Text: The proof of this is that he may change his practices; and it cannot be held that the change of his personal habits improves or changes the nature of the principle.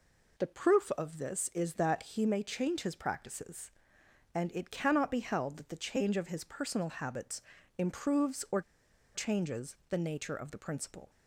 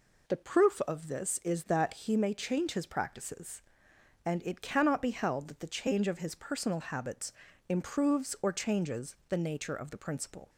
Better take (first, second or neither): second